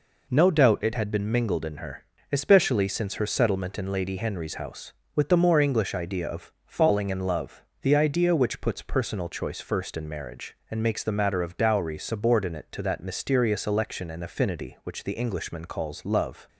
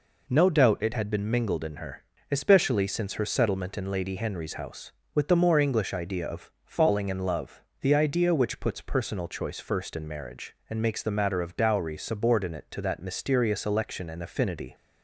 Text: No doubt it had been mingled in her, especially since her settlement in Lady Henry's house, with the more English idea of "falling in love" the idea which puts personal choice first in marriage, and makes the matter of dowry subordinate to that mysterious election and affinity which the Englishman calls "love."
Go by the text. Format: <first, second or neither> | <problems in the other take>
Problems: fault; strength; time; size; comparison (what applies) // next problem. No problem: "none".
first | pauses between "love" and "the"; slight; at 7.6 s; 0.20 s long; slight in the first // stops before "which the Englishman calls love"; at 14.7 s